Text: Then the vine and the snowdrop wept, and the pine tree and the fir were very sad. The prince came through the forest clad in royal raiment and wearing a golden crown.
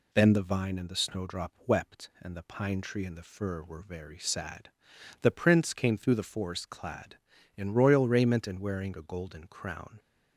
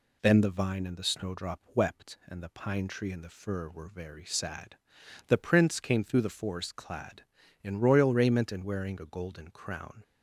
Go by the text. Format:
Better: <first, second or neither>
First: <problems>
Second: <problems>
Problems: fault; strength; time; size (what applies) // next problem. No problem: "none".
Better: neither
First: none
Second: none